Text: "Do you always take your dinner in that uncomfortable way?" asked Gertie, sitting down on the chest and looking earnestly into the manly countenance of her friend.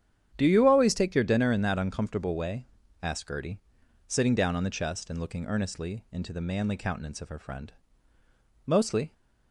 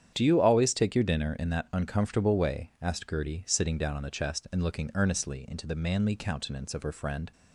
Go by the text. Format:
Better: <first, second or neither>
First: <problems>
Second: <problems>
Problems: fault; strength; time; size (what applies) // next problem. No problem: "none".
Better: second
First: starts louder than the rest; strong; until 1.3 s; 9.5 dB // goes on to say "Mostly"; slight; from 8.6 s on; 0.48 s long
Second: starts louder than the rest; strong; until 1.1 s; 8.5 dB